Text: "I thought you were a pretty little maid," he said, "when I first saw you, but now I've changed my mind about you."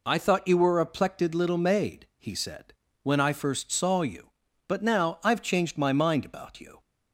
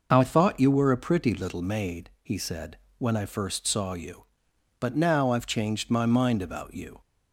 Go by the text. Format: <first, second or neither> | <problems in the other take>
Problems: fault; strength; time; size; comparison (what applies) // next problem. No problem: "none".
second | says "plected" for "pretty"; at 0.8 s